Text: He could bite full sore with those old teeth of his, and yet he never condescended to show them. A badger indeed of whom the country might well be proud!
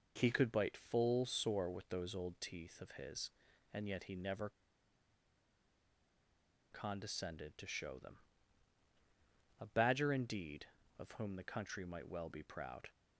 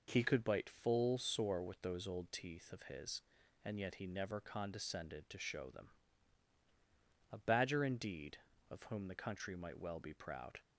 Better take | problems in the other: second | pauses between "never" and "condescended"; strong; at 4.4 s; 2.2 s long

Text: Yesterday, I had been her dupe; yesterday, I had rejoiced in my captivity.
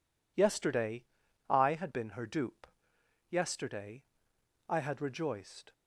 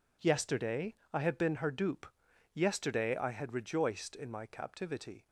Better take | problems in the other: second | stops before "in my captivity"; at 5.7 s

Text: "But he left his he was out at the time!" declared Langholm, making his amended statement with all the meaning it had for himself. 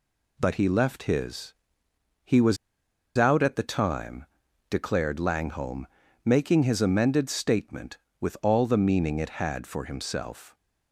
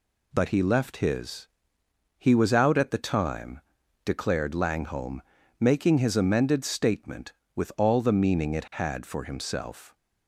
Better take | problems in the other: second | pauses between "his" and "he"; noticeable; at 1.5 s; 0.68 s long; noticeable in the second // pauses between "was" and "out"; noticeable; at 2.5 s; 0.61 s long

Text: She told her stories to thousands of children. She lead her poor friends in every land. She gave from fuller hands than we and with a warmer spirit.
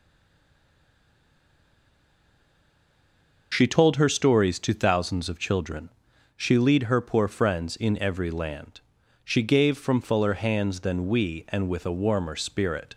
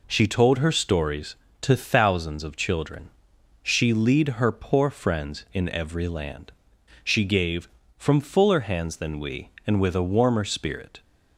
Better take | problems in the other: second | stays silent before the first word; strong; until 3.5 s; 3.5 s long

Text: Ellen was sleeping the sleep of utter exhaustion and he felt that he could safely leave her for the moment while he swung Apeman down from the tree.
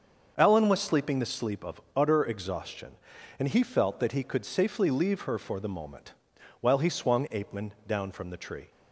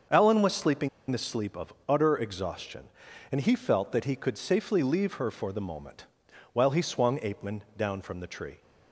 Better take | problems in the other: first | starts louder than the rest; until 1.3 s; 6.5 dB; also in the first // pauses between "sleeping" and "the"; slight; at 0.8 s; 0.21 s long // pauses between "moment" and "while"; noticeable; at 6.0 s; 0.48 s long; noticeable in the first

